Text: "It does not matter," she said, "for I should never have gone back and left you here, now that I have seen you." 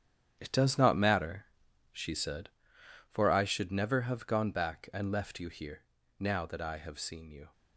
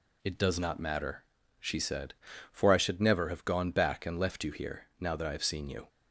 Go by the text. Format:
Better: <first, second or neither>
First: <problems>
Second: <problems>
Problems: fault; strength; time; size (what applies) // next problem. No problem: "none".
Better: second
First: gets quieter; strong; throughout; 10 dB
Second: none